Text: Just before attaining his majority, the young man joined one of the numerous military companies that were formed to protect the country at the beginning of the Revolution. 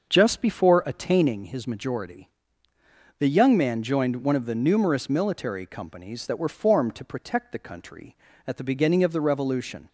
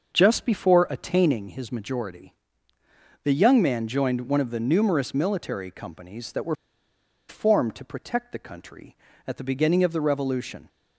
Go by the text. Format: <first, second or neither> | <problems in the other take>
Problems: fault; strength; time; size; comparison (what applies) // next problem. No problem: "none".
first | starts louder than the rest; until 1.1 s; 6.5 dB; also in the first // pauses between "were" and "formed"; noticeable; at 6.5 s; 0.74 s long